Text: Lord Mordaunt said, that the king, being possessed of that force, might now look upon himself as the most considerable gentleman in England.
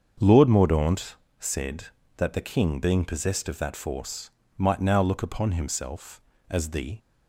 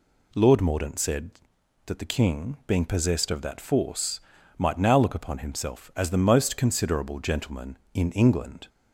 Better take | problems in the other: second | starts louder than the rest; until 1.4 s; 7 dB // pauses between "Mordaunt" and "said"; slight; at 1.1 s; 0.24 s long // stops before "most considerable gentleman in England"; at 6.9 s

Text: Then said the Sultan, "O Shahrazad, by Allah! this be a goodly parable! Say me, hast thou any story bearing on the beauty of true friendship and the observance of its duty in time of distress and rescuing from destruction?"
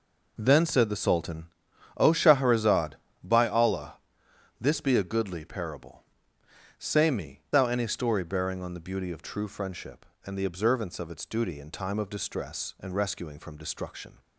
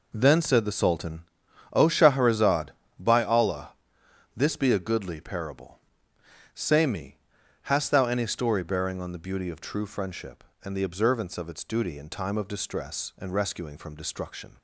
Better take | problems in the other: second | skips "hast"; at 7.4 s

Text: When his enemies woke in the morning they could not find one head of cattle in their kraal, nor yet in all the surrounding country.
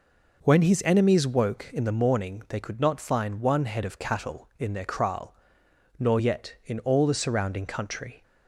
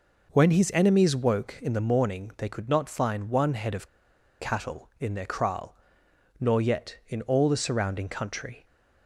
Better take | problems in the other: first | pauses between "of" and "cattle"; noticeable; at 3.8 s; 0.52 s long

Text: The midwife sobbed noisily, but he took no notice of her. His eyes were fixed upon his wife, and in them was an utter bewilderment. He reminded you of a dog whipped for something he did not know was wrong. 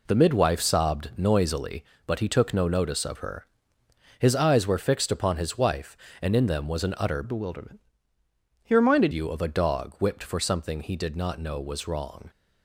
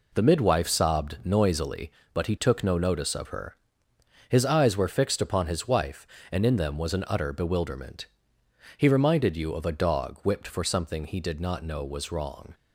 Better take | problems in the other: second | changes voice from "bewilderment" to "reminded"; from 7.2 to 9.1 s; 1.9 s long

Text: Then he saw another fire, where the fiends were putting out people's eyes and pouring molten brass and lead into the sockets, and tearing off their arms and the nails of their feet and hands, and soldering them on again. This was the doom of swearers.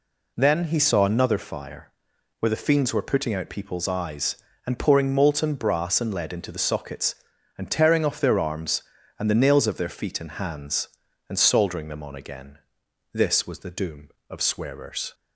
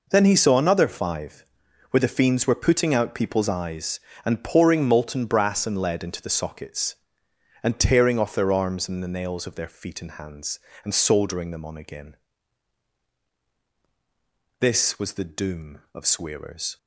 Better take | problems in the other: first | says "five" for "fire"; at 0.8 s

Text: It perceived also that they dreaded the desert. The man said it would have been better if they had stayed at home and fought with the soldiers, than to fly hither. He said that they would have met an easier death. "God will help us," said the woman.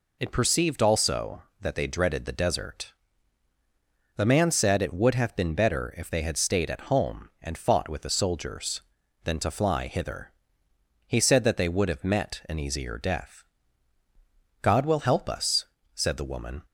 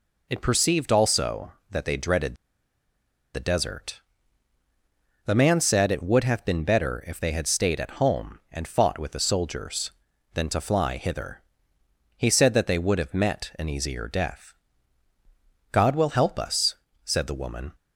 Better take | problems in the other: first | pauses between "dreaded" and "the"; at 2.3 s; 1.0 s long

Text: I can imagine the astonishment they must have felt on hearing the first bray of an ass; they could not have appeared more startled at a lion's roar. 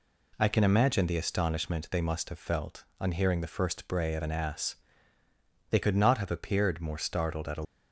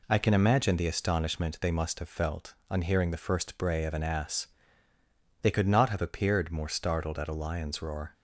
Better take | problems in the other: second | stops before "lion's roar"; at 7.6 s

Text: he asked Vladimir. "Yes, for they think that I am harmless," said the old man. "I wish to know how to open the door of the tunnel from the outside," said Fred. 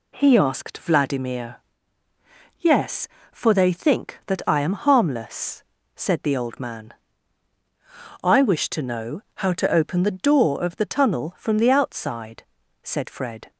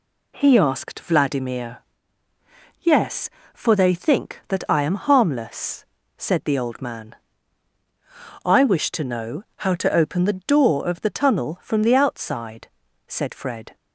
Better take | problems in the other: neither | pauses between "know" and "how"; slight; the same in both

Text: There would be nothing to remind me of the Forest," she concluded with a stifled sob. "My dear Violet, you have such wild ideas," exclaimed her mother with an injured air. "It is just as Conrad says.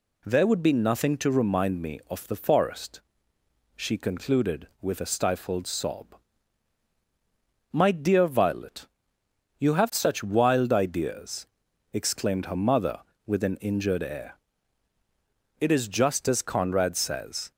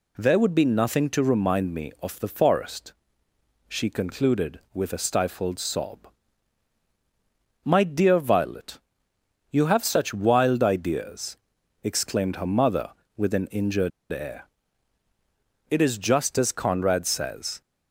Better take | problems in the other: first | pauses between "injured" and "air"; slight; at 13.9 s; 0.22 s long

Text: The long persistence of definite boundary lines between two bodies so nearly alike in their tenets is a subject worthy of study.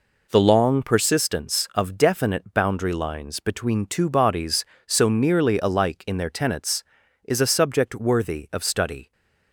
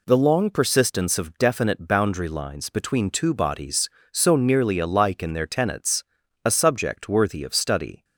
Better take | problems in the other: first | skips "is"; at 6.2 s

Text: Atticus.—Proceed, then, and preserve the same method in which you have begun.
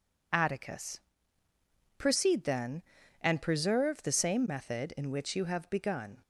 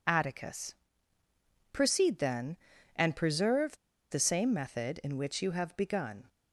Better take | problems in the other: first | pauses between "preserve" and "the"; slight; at 3.7 s; 0.34 s long

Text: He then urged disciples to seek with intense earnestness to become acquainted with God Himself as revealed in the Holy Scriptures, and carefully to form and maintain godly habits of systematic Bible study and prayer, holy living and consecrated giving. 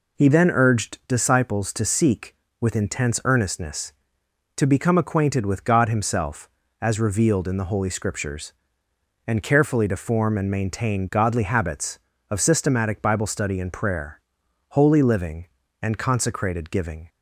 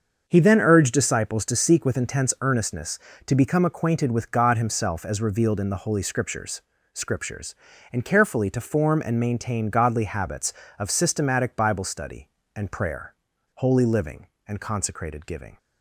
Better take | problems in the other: first | starts louder than the rest; until 1.2 s; 6.5 dB // says "Scriptures" twice; at 6.9 s

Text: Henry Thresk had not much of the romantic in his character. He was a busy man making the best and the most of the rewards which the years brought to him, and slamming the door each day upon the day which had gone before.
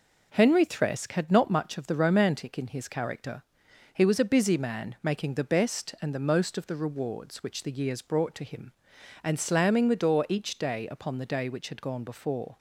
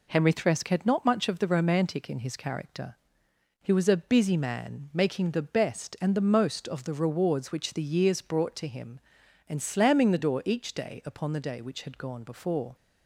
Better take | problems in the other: neither | none

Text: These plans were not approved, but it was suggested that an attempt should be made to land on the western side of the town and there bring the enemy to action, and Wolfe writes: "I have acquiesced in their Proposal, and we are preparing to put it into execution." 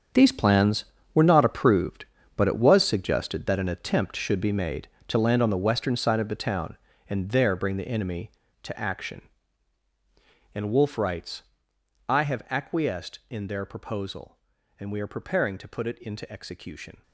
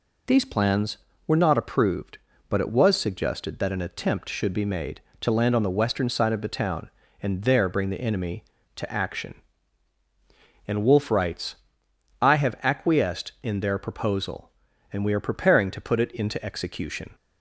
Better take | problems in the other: second | gets quieter; strong; throughout; 13.5 dB

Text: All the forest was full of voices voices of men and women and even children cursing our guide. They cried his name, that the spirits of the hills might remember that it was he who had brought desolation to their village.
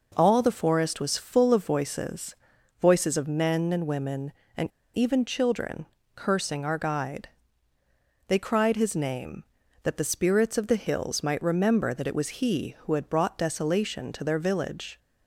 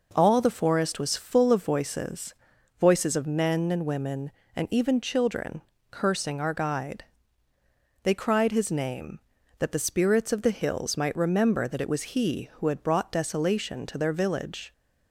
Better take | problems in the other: second | pauses between "voices" and "voices"; noticeable; at 2.3 s; 0.46 s long; noticeable in the second // pauses between "and" and "even"; slight; at 4.6 s; 0.29 s long // pauses between "children" and "cursing"; slight; at 5.8 s; 0.30 s long; slight in the second

